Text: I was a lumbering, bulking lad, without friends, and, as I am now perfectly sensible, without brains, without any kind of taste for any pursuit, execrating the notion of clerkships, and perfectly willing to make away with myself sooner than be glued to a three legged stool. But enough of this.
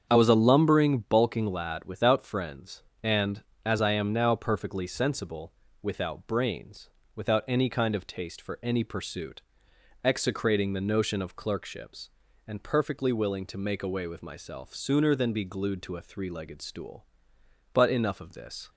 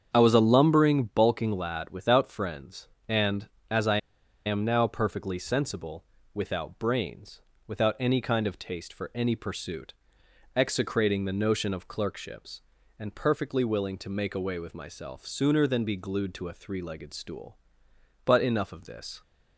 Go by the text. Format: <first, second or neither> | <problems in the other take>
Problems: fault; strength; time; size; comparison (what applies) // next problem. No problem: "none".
first | starts louder than the rest; strong; until 1.2 s; 8 dB; strong in the first // pauses between "I" and "am"; noticeable; at 3.9 s; 0.50 s long